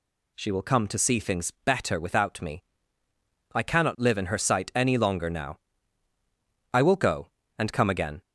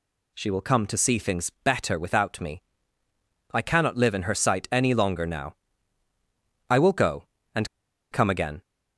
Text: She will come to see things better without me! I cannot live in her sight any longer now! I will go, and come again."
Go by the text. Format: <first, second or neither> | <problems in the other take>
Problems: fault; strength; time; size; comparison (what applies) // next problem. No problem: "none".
first | pauses between "and" and "come"; at 7.6 s; 0.43 s long